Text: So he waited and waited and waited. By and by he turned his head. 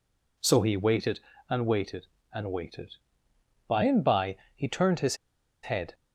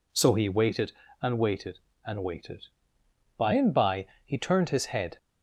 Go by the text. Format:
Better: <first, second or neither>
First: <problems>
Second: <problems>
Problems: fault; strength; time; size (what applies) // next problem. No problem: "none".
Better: second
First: pauses between "by" and "he"; slight; at 4.3 s; 0.18 s long // pauses between "his" and "head"; noticeable; at 5.1 s; 0.47 s long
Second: pauses between "by" and "he"; slight; at 4.0 s; 0.18 s long